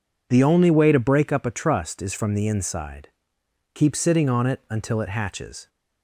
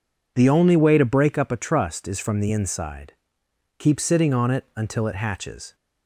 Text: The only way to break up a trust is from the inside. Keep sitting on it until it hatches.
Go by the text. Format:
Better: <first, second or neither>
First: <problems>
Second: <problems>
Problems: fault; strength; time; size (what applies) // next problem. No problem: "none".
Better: neither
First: none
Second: none